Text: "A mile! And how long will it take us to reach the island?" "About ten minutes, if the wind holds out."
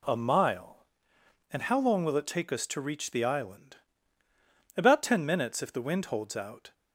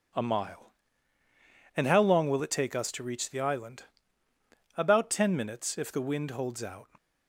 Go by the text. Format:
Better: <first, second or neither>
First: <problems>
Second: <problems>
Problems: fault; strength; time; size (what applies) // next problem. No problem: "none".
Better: neither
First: none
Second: none